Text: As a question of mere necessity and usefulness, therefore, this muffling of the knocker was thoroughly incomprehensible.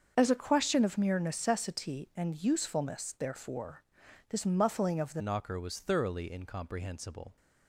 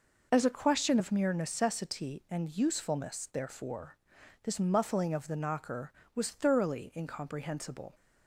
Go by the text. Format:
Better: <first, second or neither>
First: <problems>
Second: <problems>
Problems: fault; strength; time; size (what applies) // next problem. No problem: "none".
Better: second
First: starts louder than the rest; until 1.1 s; 6.5 dB // changes voice at "knocker"; from 5.1 s on; 2.2 s long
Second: none